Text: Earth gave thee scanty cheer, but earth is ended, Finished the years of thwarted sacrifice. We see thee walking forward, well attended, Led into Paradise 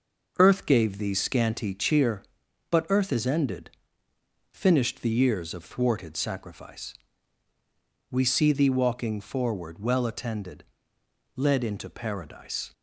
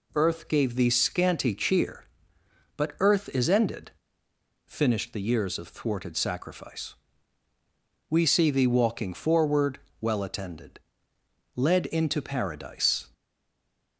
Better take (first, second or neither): first